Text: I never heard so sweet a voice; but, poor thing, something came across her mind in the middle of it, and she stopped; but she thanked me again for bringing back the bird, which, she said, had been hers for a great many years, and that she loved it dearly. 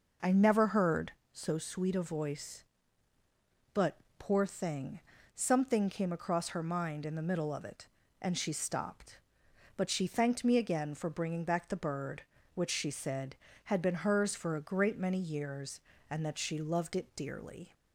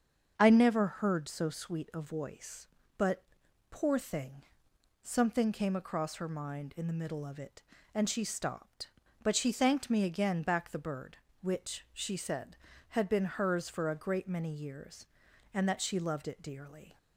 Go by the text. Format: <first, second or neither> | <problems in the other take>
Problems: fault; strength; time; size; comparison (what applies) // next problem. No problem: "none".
first | starts louder than the rest; until 1.3 s; 7 dB // skips "for bringing"; at 10.4 s